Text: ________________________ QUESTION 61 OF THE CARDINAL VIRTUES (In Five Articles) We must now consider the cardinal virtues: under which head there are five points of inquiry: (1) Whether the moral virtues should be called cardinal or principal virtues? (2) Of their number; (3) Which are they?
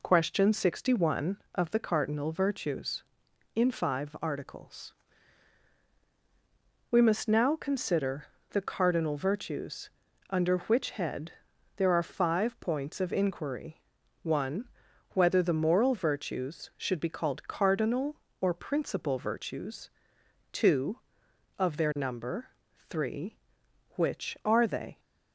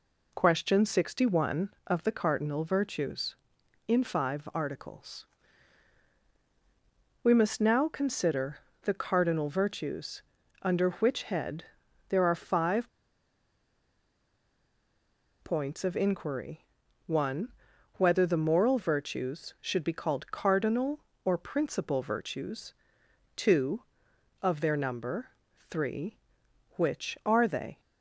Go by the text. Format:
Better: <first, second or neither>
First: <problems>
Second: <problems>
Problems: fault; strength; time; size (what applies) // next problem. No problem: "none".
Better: first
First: pauses between "consider" and "the"; slight; at 8.2 s; 0.26 s long // pauses between "head" and "there"; at 11.3 s; 0.44 s long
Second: pauses between "consider" and "the"; slight; at 8.5 s; 0.26 s long // pauses between "head" and "there"; at 11.6 s; 0.44 s long // pauses between "five" and "points"; strong; at 12.8 s; 2.5 s long